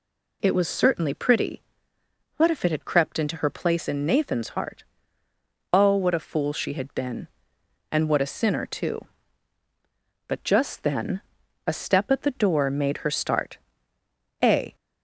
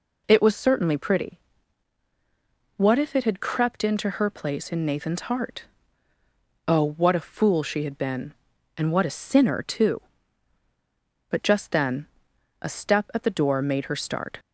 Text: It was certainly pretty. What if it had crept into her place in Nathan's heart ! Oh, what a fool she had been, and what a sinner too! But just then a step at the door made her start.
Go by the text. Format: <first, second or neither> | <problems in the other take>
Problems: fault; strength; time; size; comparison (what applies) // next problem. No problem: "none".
second | pauses between "then" and "a"; noticeable; at 11.2 s; 0.46 s long; noticeable in the second // goes on to say "A"; slight; from 14.4 s on; 0.32 s long